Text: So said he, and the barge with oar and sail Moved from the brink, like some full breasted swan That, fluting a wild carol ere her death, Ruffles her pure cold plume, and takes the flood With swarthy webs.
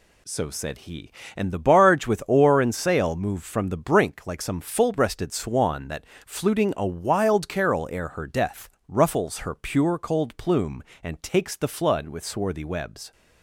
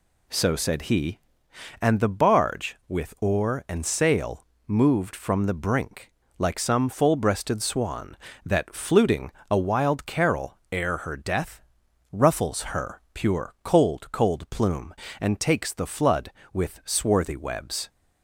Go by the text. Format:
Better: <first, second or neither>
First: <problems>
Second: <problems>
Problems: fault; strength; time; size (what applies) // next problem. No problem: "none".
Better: first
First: none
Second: pauses between "sail" and "Moved"; slight; at 4.4 s; 0.26 s long // pauses between "fluting" and "a"; slight; at 9.3 s; 0.20 s long // says "cold" twice; at 14.1 s